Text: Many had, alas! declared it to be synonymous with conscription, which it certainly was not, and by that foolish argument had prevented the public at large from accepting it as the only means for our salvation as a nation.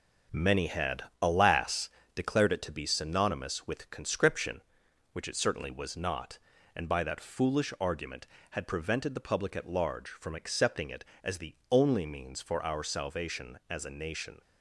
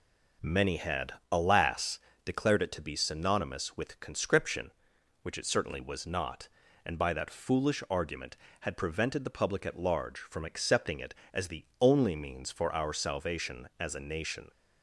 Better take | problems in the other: second | gets quieter; throughout; 6.5 dB

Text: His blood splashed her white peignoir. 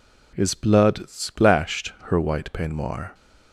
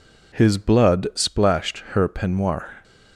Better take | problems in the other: first | skips "white"; at 2.0 s

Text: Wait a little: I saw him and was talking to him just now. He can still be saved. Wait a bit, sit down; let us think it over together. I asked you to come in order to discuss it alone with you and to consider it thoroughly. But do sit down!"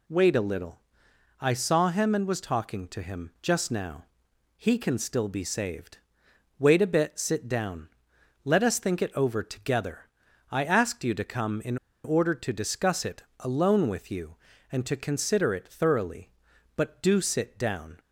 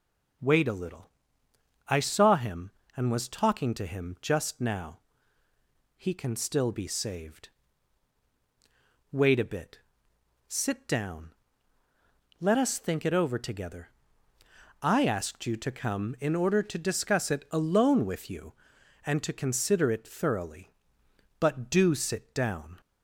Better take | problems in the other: second | pauses between "in" and "order"; slight; at 11.7 s; 0.28 s long // pauses between "it" and "alone"; slight; at 13.2 s; 0.16 s long

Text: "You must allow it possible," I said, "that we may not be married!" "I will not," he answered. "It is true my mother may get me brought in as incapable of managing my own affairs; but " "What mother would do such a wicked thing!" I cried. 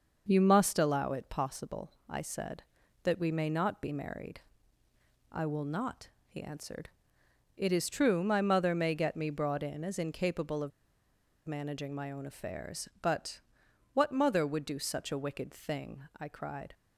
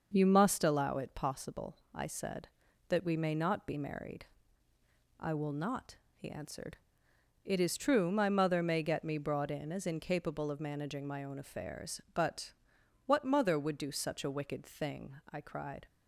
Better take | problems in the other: second | starts louder than the rest; noticeable; until 1.2 s; 6 dB; noticeable in the second // pauses between "of" and "managing"; noticeable; at 10.7 s; 0.77 s long

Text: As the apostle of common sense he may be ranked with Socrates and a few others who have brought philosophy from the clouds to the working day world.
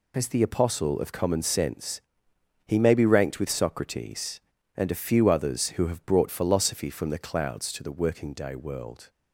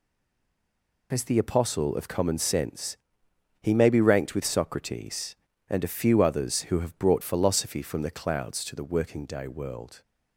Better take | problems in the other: first | stays silent before the first word; until 1.1 s; 1.1 s long // pauses between "sense" and "he"; noticeable; at 2.9 s; 0.65 s long; noticeable in the first

